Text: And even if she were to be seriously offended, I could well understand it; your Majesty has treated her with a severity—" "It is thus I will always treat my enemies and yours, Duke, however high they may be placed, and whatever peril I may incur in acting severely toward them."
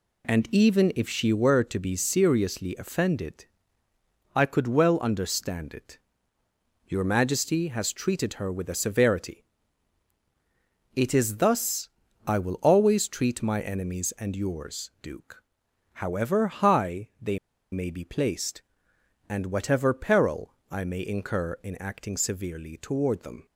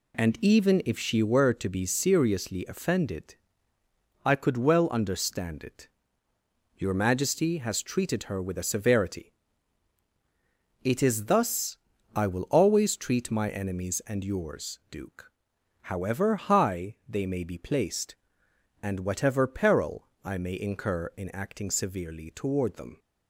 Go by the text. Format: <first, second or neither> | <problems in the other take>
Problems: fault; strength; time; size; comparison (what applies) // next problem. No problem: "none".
second | pauses between "thus" and "I"; slight; at 11.8 s; 0.36 s long; slight in the second // pauses between "they" and "may"; slight; at 17.3 s; 0.34 s long